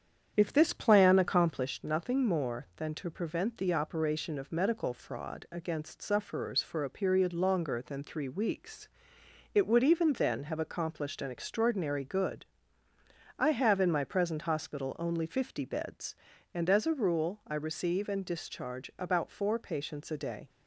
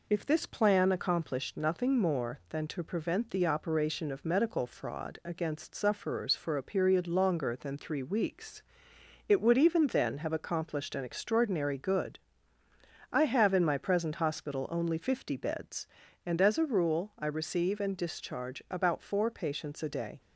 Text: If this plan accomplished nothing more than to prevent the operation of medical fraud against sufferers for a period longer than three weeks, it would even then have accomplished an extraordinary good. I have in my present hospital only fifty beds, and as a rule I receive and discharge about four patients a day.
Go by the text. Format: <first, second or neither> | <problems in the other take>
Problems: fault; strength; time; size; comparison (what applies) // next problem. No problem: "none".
second | starts louder than the rest; strong; until 1.7 s; 8 dB